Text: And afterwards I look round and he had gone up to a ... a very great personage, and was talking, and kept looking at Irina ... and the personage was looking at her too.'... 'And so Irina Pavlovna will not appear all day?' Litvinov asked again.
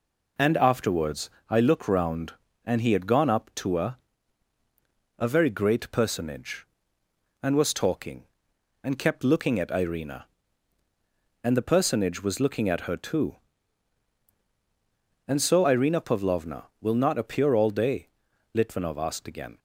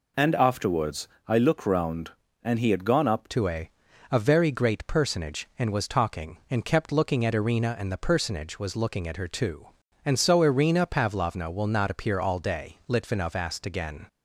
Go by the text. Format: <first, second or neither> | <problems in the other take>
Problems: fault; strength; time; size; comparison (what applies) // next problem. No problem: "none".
first | pauses between "afterwards" and "I"; slight; at 1.0 s; 0.18 s long; slight in the first // changes voice at "to"; from 3.2 s on; 10.8 s long